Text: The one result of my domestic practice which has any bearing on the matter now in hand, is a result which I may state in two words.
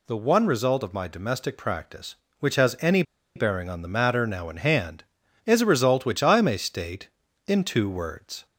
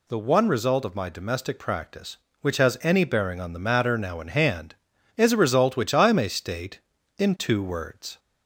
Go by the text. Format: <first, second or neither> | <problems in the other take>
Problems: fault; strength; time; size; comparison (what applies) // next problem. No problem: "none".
second | pauses between "any" and "bearing"; slight; at 3.0 s; 0.33 s long